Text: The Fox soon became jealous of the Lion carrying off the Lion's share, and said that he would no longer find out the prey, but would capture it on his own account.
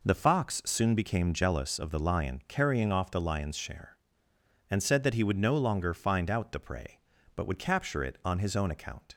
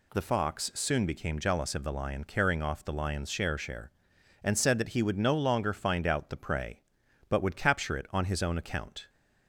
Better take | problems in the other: first | says "share" twice; at 3.5 s

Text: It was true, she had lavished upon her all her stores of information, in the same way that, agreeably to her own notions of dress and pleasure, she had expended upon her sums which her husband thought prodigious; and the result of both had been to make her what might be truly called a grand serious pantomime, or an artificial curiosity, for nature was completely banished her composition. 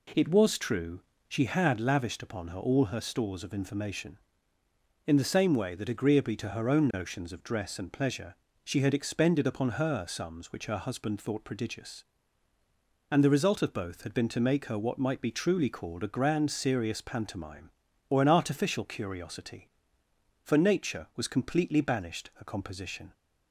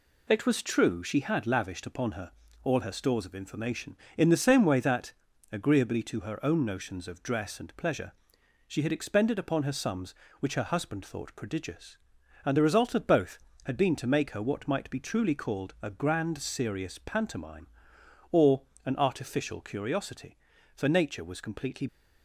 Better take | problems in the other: first | pauses between "her" and "all"; slight; at 2.3 s; 0.32 s long // pauses between "or" and "an"; slight; at 18.6 s; 0.22 s long // stops before "banished her composition"; at 21.8 s

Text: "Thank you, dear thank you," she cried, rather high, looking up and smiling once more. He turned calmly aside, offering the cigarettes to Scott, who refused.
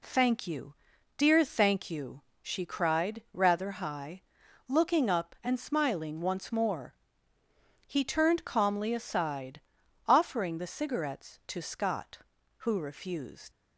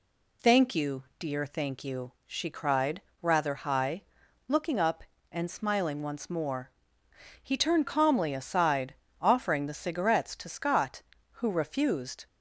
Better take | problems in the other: second | leaves "refused" unfinished; at 13.5 s; 80 ms

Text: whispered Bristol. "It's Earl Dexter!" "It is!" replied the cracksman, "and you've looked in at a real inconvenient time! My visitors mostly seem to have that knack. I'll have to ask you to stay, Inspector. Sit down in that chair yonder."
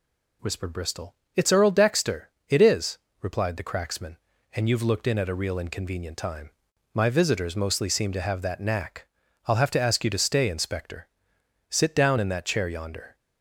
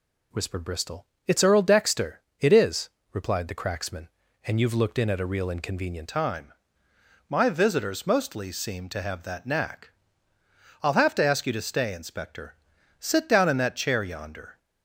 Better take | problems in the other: first | changes voice at "time"; from 6.0 s on; 8.5 s long

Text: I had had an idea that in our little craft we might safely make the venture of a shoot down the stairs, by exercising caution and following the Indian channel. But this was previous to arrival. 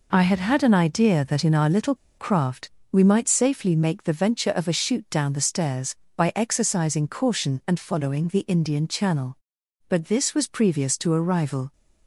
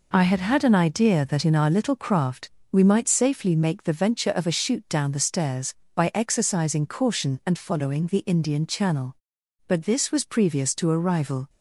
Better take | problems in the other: second | pauses between "little" and "craft"; slight; at 1.9 s; 0.22 s long // pauses between "craft" and "we"; slight; at 2.7 s; 0.20 s long; slight in the second

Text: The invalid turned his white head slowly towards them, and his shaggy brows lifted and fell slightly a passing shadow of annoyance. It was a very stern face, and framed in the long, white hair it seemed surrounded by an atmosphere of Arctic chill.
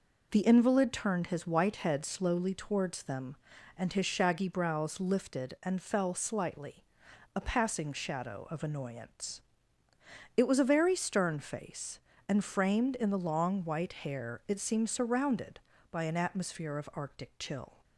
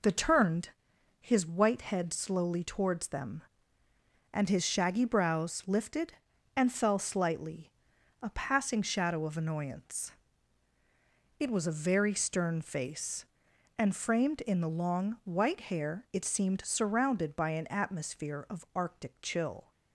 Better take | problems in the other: first | skips "invalid"; at 0.1 s // pauses between "turned" and "his"; noticeable; at 0.7 s; 0.50 s long // pauses between "slightly" and "a"; noticeable; at 7.7 s; 0.52 s long; noticeable in the first

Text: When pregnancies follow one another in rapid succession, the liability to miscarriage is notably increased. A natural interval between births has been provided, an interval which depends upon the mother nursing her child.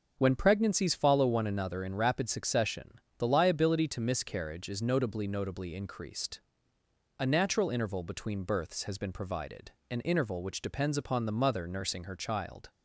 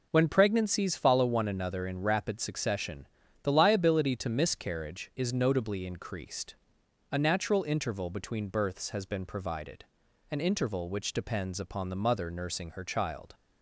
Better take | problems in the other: second | starts louder than the rest; until 1.1 s; 6.5 dB // says "notably" twice; at 5.2 s

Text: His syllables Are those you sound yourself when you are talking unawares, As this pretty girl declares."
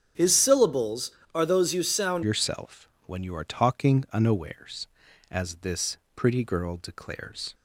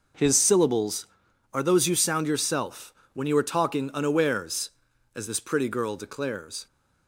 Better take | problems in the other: second | starts louder than the rest; strong; until 1.3 s; 7.5 dB // changes voice at "yourself"; from 2.2 s on; 5.3 s long // pauses between "yourself" and "when"; slight; at 2.9 s; 0.16 s long; slight in the second // pauses between "this" and "pretty"; slight; at 5.9 s; 0.18 s long

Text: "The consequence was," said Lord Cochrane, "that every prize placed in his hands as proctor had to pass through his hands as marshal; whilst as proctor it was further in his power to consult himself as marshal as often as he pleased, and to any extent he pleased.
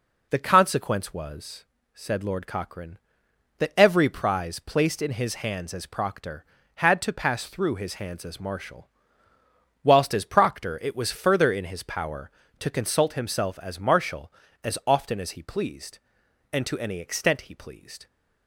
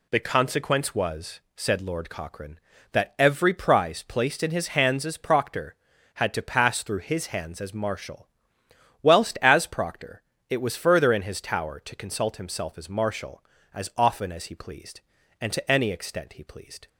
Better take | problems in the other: first | pauses between "proctor" and "it"; slight; at 10.2 s; 0.26 s long // says "tower" for "power"; at 11.4 s

